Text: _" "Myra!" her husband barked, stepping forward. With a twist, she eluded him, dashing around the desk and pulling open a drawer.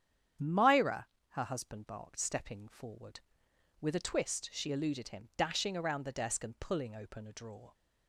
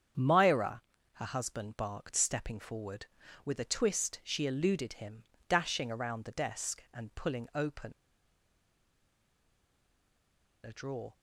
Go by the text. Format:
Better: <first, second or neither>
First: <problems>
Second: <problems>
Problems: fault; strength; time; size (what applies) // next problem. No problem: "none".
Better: first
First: starts louder than the rest; strong; until 1.6 s; 9 dB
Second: starts louder than the rest; strong; until 1.5 s; 7.5 dB // pauses between "open" and "a"; strong; at 7.9 s; 2.7 s long